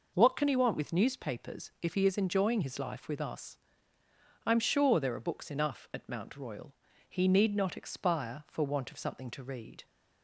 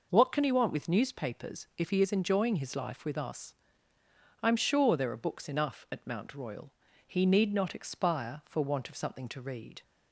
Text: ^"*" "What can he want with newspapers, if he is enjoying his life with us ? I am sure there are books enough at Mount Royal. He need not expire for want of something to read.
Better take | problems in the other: neither | none

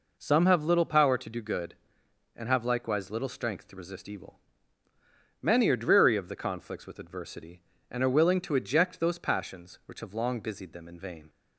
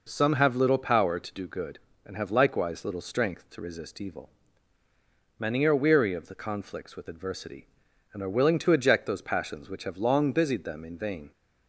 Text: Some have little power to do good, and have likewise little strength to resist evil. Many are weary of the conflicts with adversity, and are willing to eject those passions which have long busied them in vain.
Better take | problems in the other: second | says "dreary" for "weary"; at 5.7 s

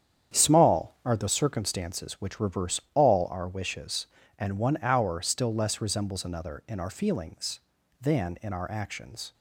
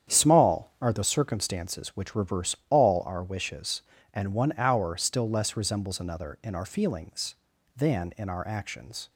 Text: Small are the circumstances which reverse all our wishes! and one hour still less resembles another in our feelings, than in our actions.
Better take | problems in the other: neither | starts louder than the rest; strong; the same in both

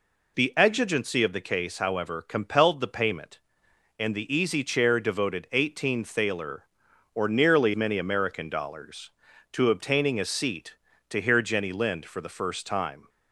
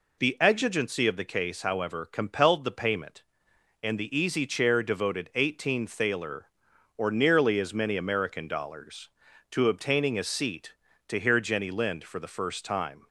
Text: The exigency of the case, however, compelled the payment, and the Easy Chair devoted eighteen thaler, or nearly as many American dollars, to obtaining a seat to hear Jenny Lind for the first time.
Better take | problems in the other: second | skips "as"; at 7.7 s

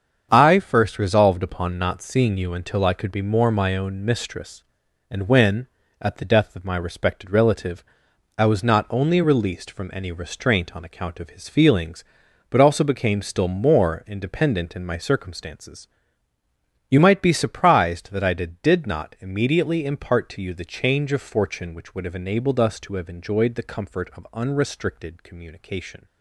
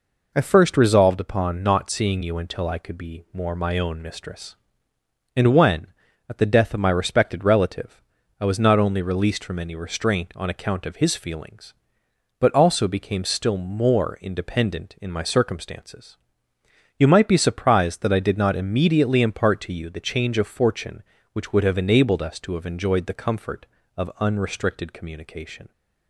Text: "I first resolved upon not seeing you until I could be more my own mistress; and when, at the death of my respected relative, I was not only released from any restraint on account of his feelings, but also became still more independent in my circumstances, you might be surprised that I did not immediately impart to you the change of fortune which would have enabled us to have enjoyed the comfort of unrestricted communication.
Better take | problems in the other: second | starts louder than the rest; strong; until 1.3 s; 7.5 dB // says "did" twice; at 18.6 s

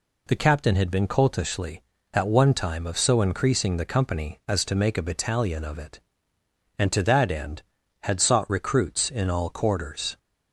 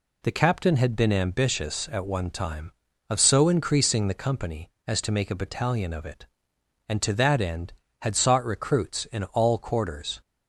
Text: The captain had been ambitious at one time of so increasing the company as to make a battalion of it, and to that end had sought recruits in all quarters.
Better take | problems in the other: second | says "coltishly" for "ambitious"; at 1.0 s

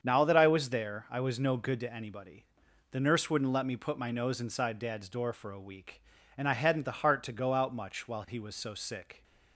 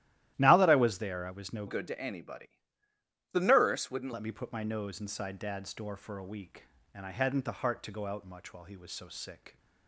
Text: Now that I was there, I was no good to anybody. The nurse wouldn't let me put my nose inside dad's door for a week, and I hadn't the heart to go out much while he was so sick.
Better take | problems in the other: first | starts louder than the rest; strong; until 1.3 s; 13.5 dB; strong in the first // changes voice from "good" to "wouldn't"; from 1.6 to 4.1 s; 2.5 s long

